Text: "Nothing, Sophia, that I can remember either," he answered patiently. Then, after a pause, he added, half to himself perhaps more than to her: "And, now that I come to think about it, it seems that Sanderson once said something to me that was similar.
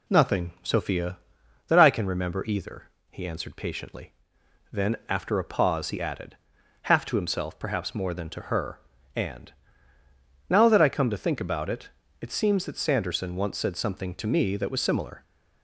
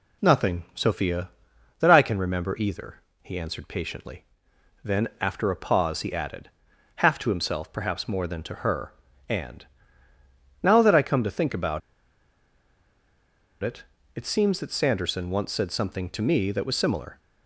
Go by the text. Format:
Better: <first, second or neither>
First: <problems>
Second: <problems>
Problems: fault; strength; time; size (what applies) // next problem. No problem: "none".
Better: first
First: none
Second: pauses between "about" and "it"; strong; at 11.8 s; 1.8 s long